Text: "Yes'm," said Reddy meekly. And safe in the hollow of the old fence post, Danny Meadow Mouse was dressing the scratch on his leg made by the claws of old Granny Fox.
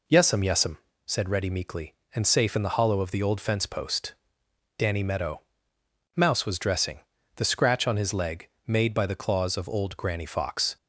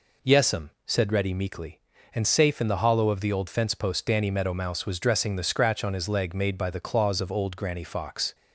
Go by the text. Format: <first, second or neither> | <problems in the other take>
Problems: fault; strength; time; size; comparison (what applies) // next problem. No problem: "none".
second | says "Yes'm" twice; at 0.4 s // pauses between "Meadow" and "Mouse"; noticeable; at 5.4 s; 0.74 s long // pauses between "dressing" and "the"; slight; at 7.0 s; 0.36 s long // pauses between "leg" and "made"; slight; at 8.4 s; 0.20 s long